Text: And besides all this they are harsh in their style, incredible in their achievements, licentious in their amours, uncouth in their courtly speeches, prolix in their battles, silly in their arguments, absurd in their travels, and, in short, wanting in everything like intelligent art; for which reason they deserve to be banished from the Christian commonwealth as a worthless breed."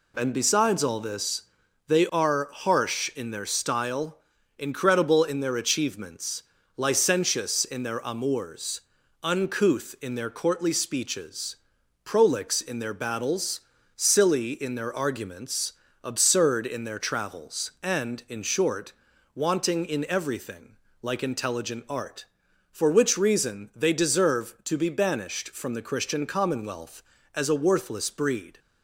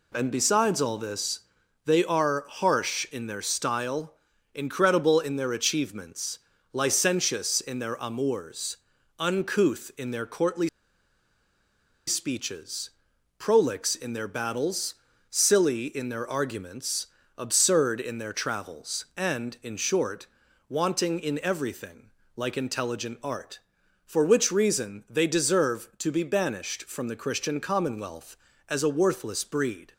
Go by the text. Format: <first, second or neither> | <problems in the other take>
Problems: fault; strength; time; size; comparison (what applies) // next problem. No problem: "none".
first | pauses between "this" and "they"; at 1.4 s; 0.44 s long; also in the first // pauses between "courtly" and "speeches"; strong; at 10.6 s; 1.3 s long // pauses between "everything" and "like"; slight; at 22.0 s; 0.26 s long; slight in the first